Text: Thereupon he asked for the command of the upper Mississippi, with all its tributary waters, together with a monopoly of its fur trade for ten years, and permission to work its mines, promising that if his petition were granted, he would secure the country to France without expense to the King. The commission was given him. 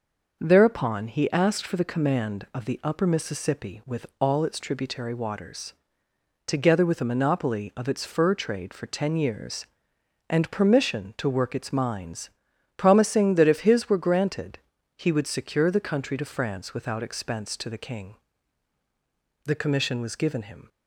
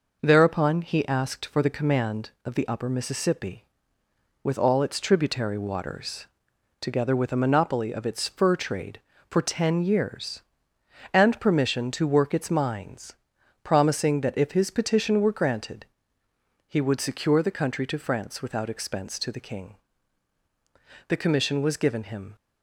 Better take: second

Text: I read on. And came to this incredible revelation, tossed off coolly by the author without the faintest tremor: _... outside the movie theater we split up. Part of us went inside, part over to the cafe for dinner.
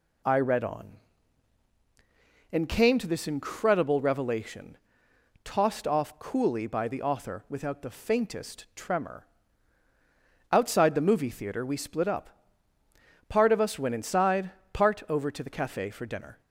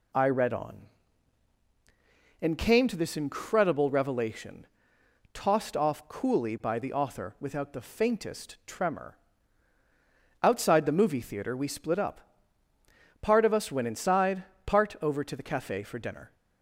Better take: neither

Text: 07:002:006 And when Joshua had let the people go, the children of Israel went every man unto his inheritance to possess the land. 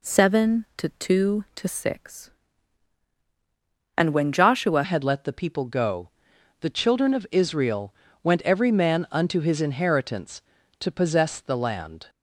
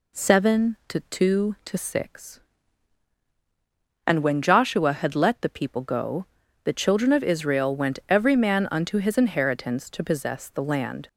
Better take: second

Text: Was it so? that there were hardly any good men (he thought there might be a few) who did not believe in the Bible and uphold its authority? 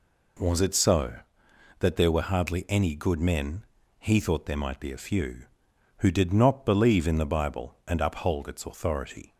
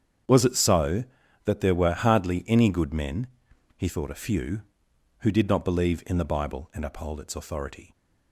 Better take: first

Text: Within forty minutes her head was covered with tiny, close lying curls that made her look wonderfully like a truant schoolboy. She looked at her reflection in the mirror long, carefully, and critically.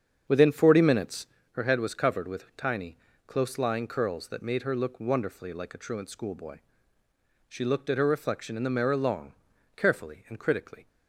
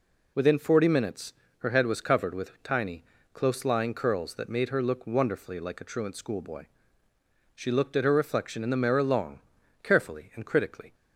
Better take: second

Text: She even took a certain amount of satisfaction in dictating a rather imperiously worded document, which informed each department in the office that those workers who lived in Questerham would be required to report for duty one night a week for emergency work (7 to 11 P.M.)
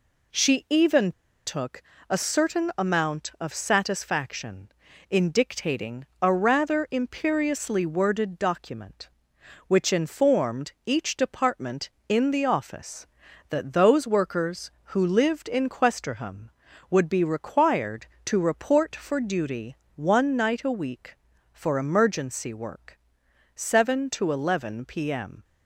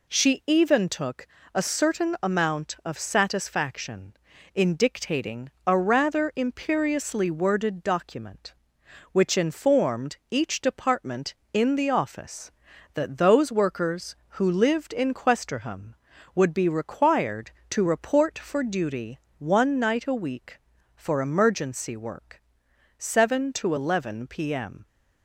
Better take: second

